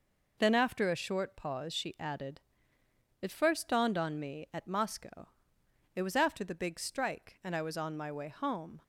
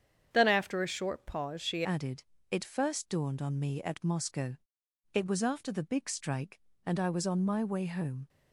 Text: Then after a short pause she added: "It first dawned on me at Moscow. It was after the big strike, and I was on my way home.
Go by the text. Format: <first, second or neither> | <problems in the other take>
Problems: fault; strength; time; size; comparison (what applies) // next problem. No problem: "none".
first | starts louder than the rest; strong; until 1.3 s; 8.5 dB // changes voice at "added"; from 1.8 s on; 6.4 s long